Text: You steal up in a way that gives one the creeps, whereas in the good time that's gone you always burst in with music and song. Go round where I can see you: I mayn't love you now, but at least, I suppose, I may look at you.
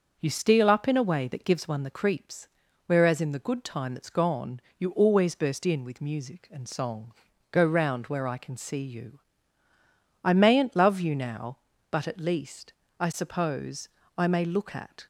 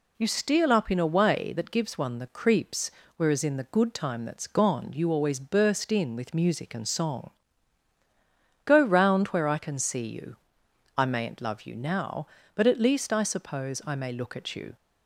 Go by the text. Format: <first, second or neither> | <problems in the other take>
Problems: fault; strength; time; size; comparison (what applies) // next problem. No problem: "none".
second | starts louder than the rest; until 1.2 s; 6.5 dB // pauses between "gone" and "you"; slight; at 4.5 s; 0.18 s long // stops before "you"; at 15.0 s